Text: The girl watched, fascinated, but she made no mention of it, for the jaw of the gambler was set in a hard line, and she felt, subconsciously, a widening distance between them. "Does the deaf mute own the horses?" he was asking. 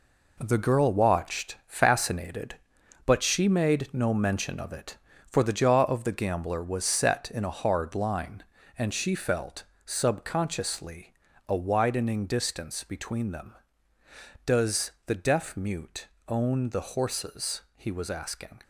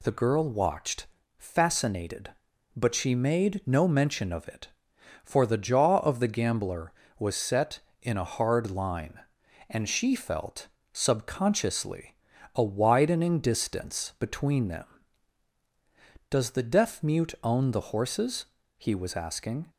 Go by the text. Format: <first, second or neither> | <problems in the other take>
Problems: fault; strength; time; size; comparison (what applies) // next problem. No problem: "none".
second | gets quieter; strong; throughout; 8 dB // pauses between "mute" and "own"; slight; at 16.0 s; 0.22 s long